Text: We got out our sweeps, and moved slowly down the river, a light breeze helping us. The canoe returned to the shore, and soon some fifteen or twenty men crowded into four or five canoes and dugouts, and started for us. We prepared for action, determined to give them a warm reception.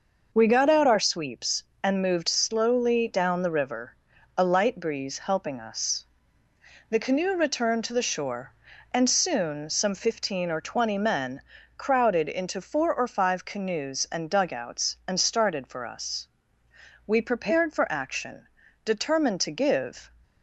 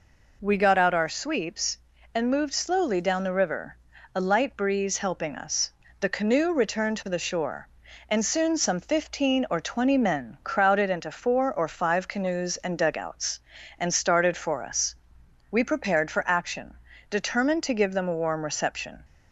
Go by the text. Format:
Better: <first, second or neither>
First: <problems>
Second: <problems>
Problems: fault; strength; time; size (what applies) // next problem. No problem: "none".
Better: second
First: pauses between "men" and "crowded"; slight; at 11.4 s; 0.34 s long // stops before "them a warm reception"; at 20.2 s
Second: none